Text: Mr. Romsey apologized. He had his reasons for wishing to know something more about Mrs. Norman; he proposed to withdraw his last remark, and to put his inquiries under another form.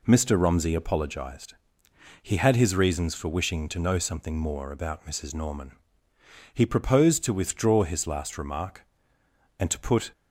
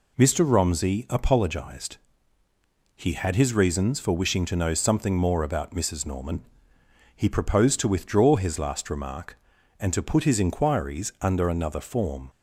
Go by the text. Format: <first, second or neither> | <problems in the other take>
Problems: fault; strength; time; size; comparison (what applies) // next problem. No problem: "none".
second | stops before "his inquiries under another form"; at 10.1 s